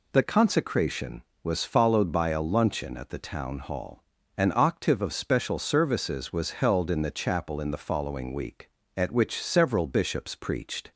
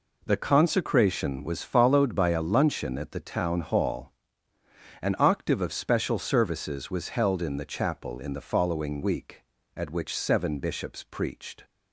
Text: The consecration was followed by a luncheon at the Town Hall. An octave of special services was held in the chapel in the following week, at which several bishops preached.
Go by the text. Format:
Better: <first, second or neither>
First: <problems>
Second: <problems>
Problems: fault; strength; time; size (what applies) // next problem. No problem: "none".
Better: first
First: none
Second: says "seven" for "several"; at 10.1 s